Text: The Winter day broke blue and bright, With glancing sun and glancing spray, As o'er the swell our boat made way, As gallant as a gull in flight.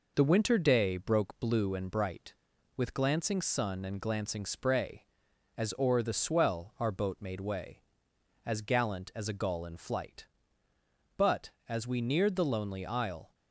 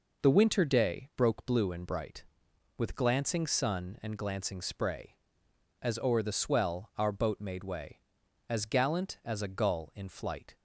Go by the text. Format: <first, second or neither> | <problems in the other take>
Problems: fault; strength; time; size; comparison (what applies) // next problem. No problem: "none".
second | goes on to say "But as we neared the lonely Isle"; strong; from 11.1 s on; 2.1 s long